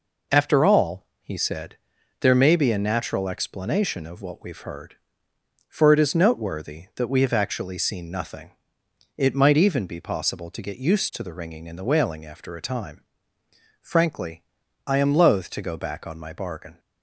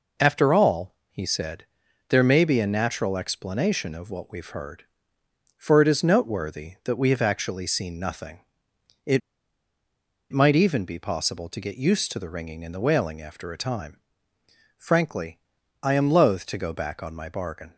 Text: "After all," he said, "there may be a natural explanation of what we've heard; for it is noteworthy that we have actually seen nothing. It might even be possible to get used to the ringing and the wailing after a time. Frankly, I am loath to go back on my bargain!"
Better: first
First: none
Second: pauses between "It" and "might"; at 9.2 s; 1.1 s long

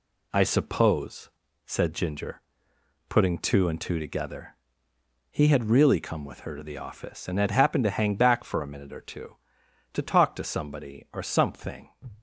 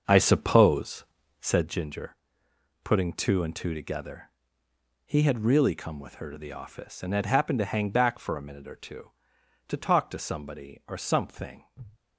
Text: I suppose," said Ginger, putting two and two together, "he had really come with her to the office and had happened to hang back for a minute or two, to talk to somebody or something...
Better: first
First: none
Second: starts louder than the rest; until 1.7 s; 6.5 dB

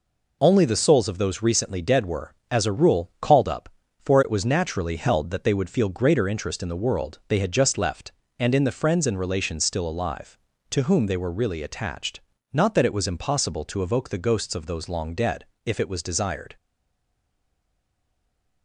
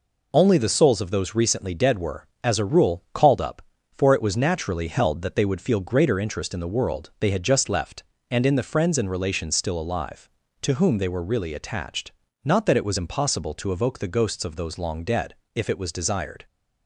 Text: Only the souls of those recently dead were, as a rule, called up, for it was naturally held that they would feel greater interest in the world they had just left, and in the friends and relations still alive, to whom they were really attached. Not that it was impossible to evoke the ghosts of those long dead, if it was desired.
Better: second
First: stays silent after the last word; from 16.5 s on; 2.1 s long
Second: none

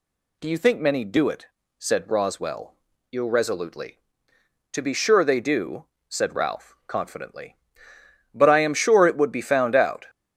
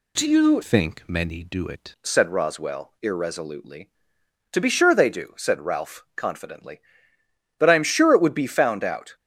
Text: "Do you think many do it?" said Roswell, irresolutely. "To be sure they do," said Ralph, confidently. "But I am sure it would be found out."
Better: first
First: none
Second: changes voice from "think" to "it"; from 0.6 to 1.9 s; 1.3 s long

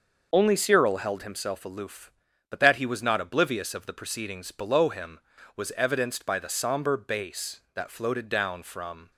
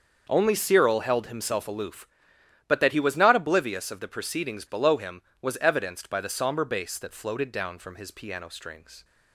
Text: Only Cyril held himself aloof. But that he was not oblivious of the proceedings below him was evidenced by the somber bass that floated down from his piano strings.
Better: second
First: starts louder than the rest; noticeable; until 1.3 s; 6 dB // stops before "his piano strings"; at 9.1 s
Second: starts louder than the rest; until 1.2 s; 6.5 dB

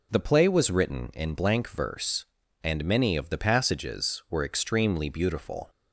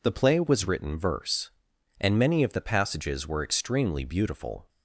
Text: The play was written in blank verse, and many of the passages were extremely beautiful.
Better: first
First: none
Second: skips "in blank"; at 0.9 s

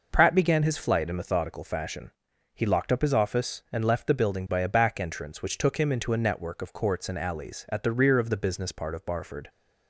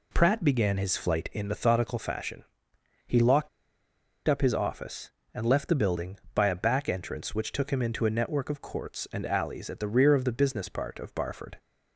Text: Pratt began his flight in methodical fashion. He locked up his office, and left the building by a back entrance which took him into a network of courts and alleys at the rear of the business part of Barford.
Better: first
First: none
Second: pauses between "locked" and "up"; noticeable; at 3.4 s; 0.78 s long

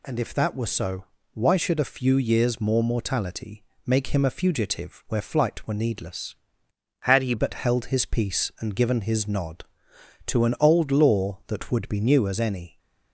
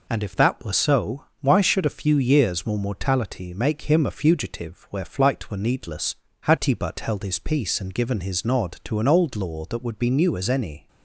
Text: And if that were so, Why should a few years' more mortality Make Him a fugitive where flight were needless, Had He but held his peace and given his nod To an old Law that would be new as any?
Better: second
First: pauses between "mortality" and "Make"; slight; at 3.6 s; 0.22 s long // changes voice from "Had" to "He"; from 7.0 to 7.3 s; 0.3 s long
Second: none

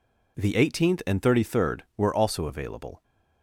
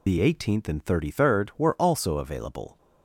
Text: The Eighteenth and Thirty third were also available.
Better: first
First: none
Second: loses the start of "The"; at 0.0 s; 90 ms

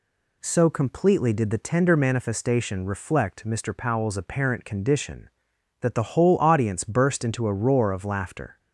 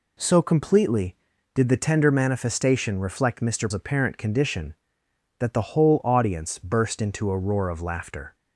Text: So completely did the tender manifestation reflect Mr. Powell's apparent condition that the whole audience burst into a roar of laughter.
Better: first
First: none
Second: skips "Powell's"; at 3.7 s

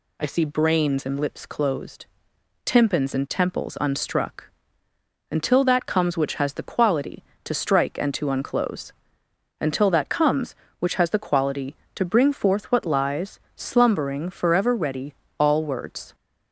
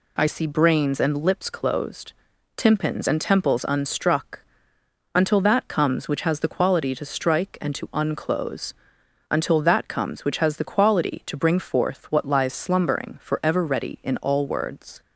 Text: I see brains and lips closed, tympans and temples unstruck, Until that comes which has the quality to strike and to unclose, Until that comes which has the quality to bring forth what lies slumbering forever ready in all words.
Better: second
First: pauses between "lies" and "slumbering"; slight; at 13.3 s; 0.16 s long // skips "in"; at 15.2 s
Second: none

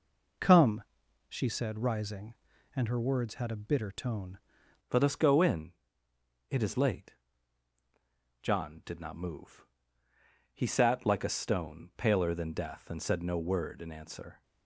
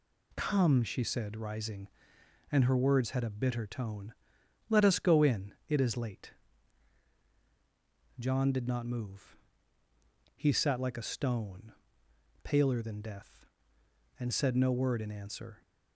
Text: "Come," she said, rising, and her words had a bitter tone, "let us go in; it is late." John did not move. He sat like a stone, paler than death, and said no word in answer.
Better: second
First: changes voice at "let"; from 4.9 s on; 9.5 s long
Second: none

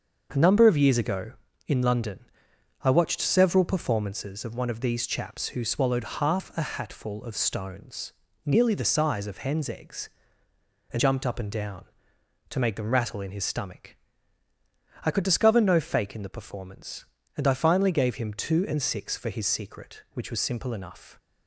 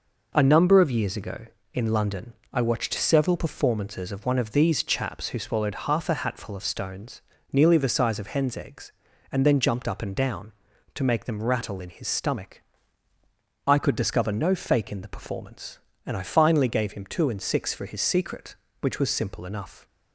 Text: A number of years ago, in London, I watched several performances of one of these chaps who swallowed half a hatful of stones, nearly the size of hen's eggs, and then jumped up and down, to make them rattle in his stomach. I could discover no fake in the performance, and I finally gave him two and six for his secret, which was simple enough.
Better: second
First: starts louder than the rest; until 1.3 s; 6.5 dB // skips "then"; at 10.9 s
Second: none

